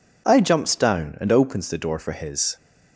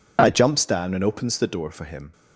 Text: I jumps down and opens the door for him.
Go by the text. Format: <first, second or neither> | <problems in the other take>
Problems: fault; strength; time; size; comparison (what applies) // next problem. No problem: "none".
second | says "his" for "him"; at 2.1 s